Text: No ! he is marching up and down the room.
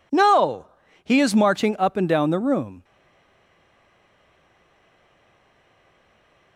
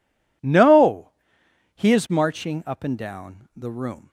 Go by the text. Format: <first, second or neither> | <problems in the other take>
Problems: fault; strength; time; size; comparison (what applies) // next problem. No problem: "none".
second | stays silent after the last word; strong; from 2.8 s on; 3.7 s long